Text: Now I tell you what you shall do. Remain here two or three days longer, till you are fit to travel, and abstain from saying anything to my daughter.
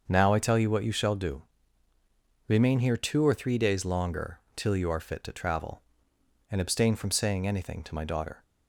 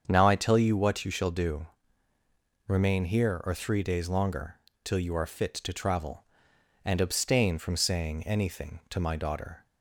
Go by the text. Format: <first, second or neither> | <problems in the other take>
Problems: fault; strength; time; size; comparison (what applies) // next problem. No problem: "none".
first | starts louder than the rest; strong; until 1.0 s; 7.5 dB; also in the first // skips "two"; at 3.4 s